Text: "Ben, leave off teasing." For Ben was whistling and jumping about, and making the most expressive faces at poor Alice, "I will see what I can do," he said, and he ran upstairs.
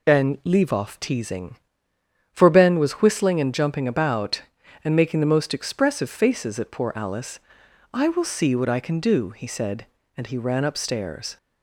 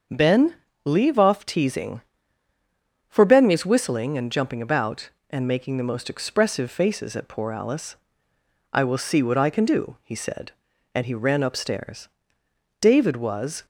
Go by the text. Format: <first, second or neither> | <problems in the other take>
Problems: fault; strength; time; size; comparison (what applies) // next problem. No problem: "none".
first | starts louder than the rest; until 1.4 s; 6.5 dB // goes on to say "David was"; noticeable; from 12.8 s on; 0.84 s long